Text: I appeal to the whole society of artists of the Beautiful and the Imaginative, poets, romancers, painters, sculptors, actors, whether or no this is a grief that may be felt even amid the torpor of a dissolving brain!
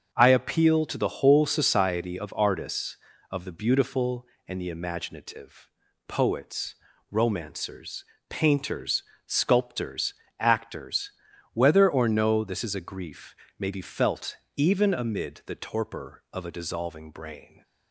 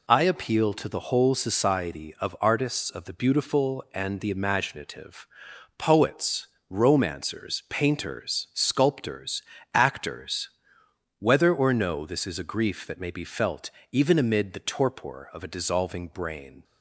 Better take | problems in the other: second | starts louder than the rest; until 1.1 s; 7 dB // skips "that"; at 13.4 s // pauses between "felt" and "even"; slight; at 14.3 s; 0.22 s long; slight in the second

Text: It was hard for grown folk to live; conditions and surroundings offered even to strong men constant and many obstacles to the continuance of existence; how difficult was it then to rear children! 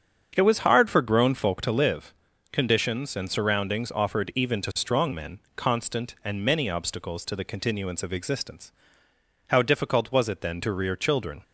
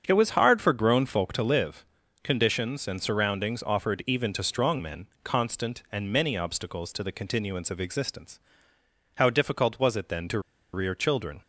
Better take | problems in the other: first | starts louder than the rest; strong; until 1.0 s; 7.5 dB; strong in the first // pauses between "men" and "constant"; slight; at 5.0 s; 0.16 s long; slight in the first // pauses between "to" and "rear"; slight; at 10.3 s; 0.34 s long

